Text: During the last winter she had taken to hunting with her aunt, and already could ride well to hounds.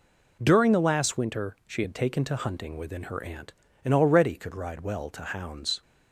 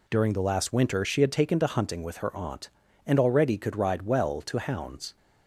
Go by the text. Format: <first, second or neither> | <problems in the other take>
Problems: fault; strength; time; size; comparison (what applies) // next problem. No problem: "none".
second | says "within" for "with"; at 2.7 s